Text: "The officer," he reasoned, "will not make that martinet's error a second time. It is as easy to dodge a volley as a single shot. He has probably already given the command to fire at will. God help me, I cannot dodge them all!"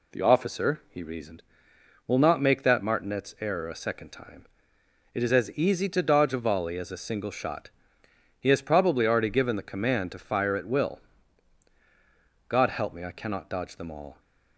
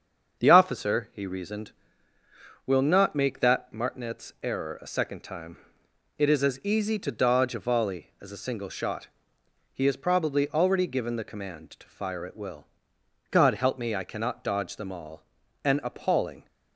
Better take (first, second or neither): first